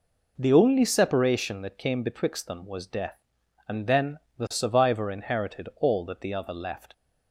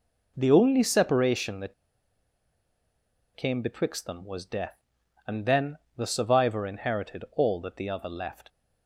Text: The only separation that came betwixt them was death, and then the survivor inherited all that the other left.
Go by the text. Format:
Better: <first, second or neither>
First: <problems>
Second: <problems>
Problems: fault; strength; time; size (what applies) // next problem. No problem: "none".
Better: first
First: pauses between "then" and "the"; slight; at 4.1 s; 0.18 s long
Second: pauses between "that" and "came"; strong; at 1.7 s; 1.6 s long // pauses between "then" and "the"; slight; at 5.7 s; 0.18 s long